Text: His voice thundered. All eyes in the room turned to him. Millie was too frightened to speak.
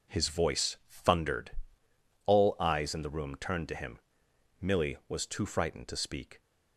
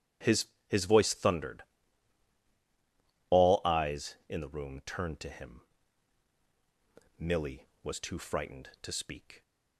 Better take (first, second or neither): first